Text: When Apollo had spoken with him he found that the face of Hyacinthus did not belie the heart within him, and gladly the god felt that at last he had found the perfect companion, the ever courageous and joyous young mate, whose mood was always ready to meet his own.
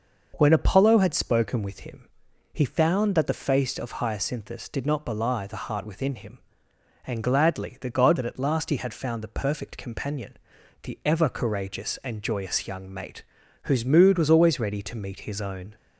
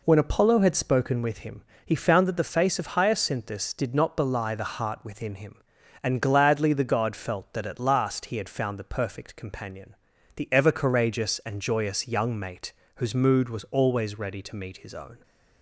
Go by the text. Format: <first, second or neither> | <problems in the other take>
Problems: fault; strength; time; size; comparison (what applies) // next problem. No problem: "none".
second | pauses between "him" and "he"; at 2.0 s; 0.44 s long; slight in the second // skips "felt"; at 8.1 s